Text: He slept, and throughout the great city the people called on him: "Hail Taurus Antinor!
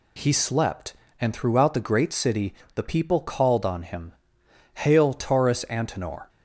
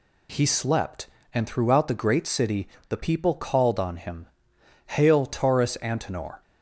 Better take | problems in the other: neither | pauses between "city" and "the"; slight; the same in both

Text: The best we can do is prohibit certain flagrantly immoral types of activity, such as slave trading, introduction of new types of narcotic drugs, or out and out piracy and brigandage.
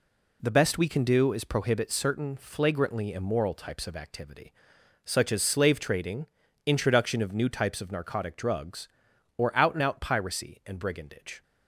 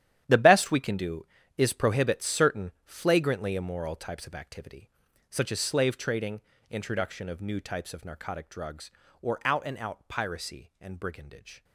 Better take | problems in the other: first | gets quieter; strong; throughout; 14 dB

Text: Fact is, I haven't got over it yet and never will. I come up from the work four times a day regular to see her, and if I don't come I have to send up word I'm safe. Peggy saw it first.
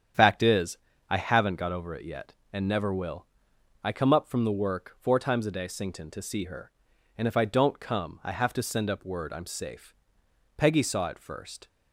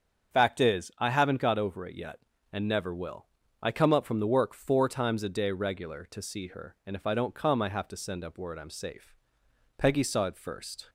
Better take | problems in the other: second | starts louder than the rest; strong; until 1.4 s; 8.5 dB; strong in the second // says "sington" for "regular"; at 5.6 s

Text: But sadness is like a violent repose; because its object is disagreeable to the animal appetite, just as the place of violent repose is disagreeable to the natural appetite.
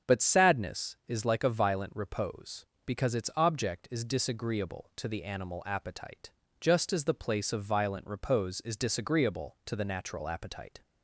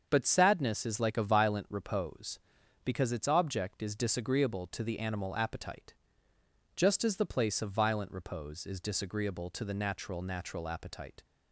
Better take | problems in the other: first | starts louder than the rest; until 1.1 s; 7 dB; strong in the first // says "natural" twice; at 10.2 s

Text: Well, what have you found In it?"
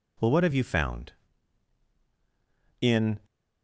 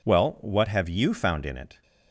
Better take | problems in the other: second | stops before "it"; at 3.2 s

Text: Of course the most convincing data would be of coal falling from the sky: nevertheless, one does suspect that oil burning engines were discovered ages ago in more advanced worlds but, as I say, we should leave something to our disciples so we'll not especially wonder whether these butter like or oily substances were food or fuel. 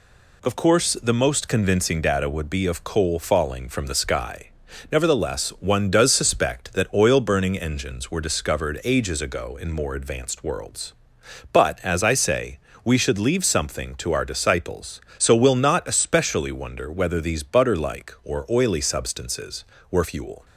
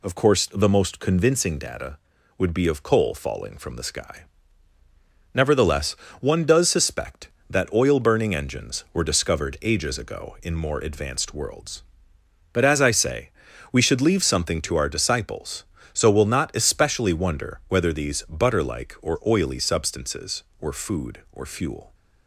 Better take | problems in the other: second | skips "food or"; at 20.0 s

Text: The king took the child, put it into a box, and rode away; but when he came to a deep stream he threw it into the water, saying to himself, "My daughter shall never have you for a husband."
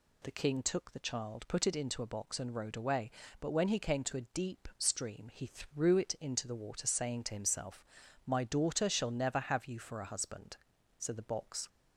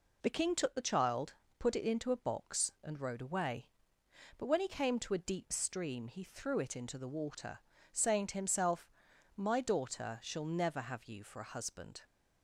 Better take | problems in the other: second | goes on to say "So the box"; noticeable; from 10.9 s on; 0.70 s long

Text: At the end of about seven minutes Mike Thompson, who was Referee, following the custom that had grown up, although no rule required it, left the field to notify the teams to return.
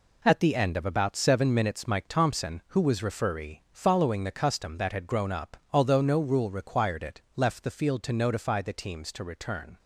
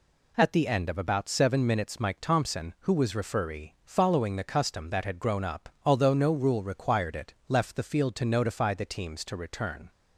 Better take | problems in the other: second | gets quieter; strong; throughout; 8 dB

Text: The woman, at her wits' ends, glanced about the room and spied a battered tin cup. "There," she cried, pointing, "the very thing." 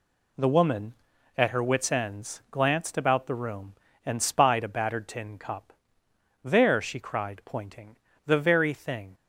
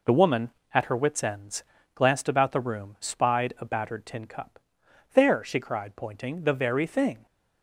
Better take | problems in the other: first | skips "and"; at 2.9 s

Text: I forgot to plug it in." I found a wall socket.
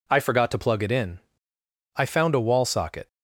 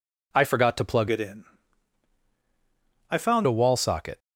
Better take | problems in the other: first | changes voice from "it" to "found"; from 1.0 to 3.4 s; 2.4 s long

